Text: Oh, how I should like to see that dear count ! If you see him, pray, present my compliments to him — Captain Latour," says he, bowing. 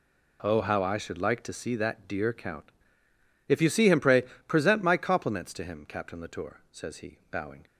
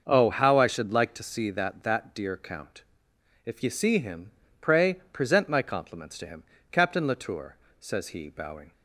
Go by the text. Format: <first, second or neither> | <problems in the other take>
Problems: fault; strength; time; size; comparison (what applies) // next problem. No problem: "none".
first | starts louder than the rest; until 1.0 s; 6 dB // says "that" twice; at 1.8 s